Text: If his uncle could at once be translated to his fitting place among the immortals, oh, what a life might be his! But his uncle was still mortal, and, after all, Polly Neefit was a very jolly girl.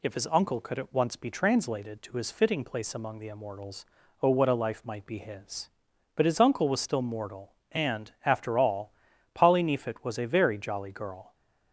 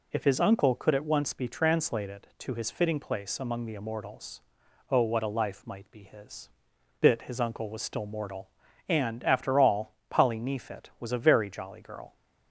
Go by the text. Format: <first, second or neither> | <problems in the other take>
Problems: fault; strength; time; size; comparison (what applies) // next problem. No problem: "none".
first | says "Bit" for "But"; at 7.0 s